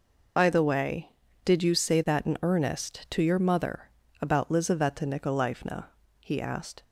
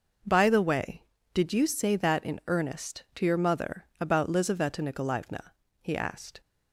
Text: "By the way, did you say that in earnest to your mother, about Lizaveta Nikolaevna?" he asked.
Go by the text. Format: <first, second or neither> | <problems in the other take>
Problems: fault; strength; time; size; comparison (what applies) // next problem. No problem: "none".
second | loses the start of "By"; at 0.3 s; 50 ms